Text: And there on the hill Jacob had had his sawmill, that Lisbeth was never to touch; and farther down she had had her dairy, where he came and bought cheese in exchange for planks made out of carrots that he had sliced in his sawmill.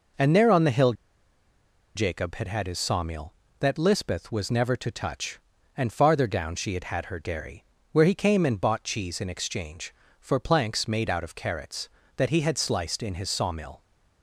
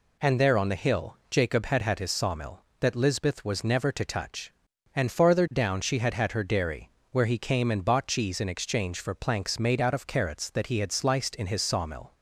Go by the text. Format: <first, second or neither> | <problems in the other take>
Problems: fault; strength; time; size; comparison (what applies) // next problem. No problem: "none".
second | pauses between "hill" and "Jacob"; at 0.9 s; 1.0 s long